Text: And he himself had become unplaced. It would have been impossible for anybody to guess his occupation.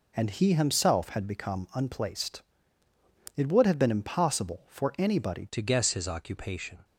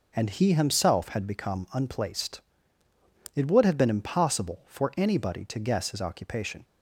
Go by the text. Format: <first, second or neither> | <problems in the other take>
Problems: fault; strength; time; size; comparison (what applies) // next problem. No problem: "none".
second | changes voice at "to"; from 5.5 s on; 1.3 s long